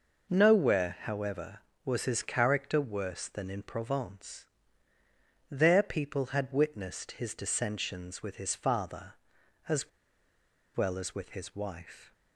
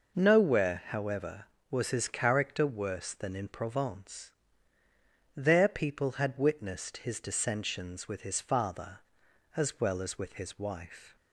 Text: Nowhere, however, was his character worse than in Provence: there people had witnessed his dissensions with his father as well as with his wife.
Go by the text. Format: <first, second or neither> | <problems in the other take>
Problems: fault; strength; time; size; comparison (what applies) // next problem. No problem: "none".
second | pauses between "as" and "well"; noticeable; at 9.8 s; 0.86 s long